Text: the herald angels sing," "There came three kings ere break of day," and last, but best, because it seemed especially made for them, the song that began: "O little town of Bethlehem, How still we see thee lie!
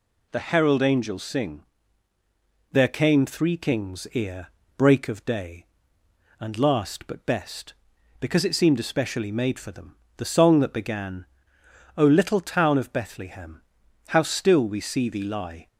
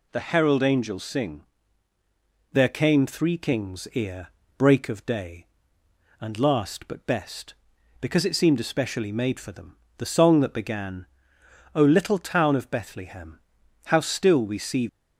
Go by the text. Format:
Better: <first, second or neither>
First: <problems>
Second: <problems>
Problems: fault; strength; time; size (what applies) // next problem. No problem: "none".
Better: first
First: pauses between "ere" and "break"; slight; at 4.4 s; 0.28 s long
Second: pauses between "ere" and "break"; slight; at 4.2 s; 0.28 s long // stops before "thee lie"; at 14.8 s